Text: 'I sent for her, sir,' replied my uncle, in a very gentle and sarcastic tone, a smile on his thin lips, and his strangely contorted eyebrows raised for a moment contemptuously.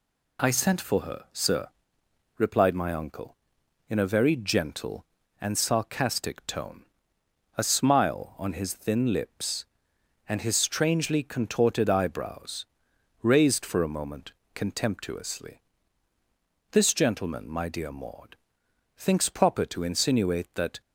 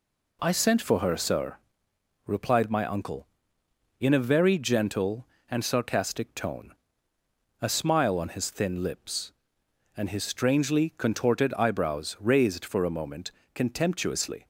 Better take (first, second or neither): second